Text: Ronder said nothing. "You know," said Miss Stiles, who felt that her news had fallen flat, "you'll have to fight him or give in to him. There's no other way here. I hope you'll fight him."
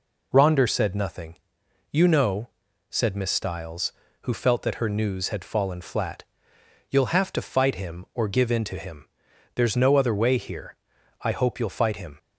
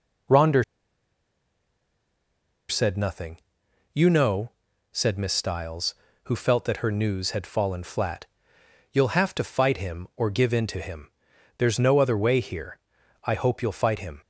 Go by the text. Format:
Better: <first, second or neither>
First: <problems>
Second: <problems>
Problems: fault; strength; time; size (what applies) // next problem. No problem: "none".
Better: first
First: none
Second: pauses between "Ronder" and "said"; strong; at 0.6 s; 2.0 s long